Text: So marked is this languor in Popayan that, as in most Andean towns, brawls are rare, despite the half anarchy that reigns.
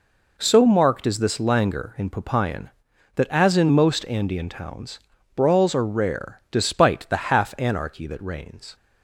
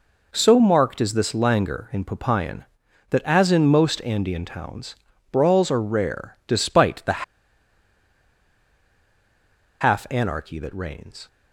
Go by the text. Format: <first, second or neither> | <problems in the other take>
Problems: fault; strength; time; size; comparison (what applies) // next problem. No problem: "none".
first | pauses between "the" and "half"; strong; at 7.2 s; 2.5 s long